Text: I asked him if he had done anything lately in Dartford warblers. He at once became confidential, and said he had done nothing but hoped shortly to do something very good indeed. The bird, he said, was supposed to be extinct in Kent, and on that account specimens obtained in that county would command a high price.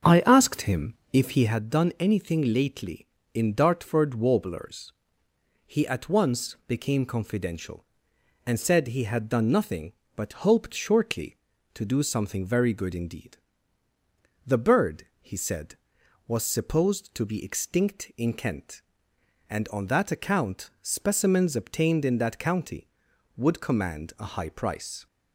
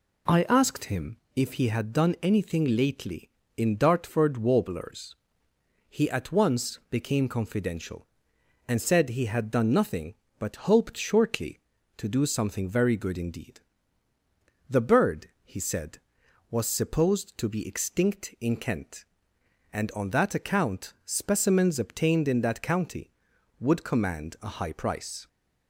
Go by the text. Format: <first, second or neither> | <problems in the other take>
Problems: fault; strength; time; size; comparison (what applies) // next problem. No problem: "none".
second | starts louder than the rest; until 1.6 s; 6.5 dB // pauses between "him" and "if"; slight; at 0.9 s; 0.18 s long; slight in the second